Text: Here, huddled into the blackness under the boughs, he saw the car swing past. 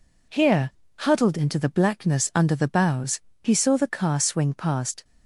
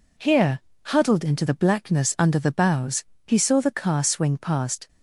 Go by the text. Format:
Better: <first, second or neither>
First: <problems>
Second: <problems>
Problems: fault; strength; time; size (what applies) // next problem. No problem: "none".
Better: neither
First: none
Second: none